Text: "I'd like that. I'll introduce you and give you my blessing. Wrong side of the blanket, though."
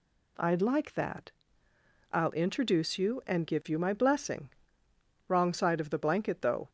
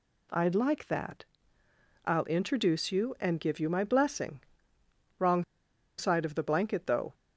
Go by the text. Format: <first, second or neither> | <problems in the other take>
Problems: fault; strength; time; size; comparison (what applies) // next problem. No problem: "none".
first | pauses between "Wrong" and "side"; noticeable; at 5.4 s; 0.54 s long